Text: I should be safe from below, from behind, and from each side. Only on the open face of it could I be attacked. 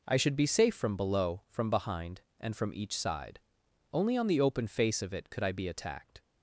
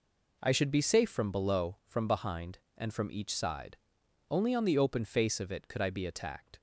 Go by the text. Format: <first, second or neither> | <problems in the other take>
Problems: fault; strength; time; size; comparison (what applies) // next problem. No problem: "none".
neither | none